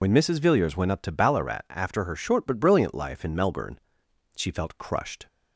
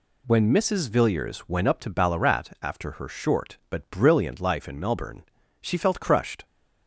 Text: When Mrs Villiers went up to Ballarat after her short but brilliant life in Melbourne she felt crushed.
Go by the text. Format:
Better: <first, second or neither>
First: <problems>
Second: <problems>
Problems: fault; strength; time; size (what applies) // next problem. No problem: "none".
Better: second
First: loses the start of "When"; at 0.0 s; 65 ms // pauses between "Melbourne" and "she"; noticeable; at 3.7 s; 0.56 s long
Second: pauses between "Melbourne" and "she"; at 5.2 s; 0.40 s long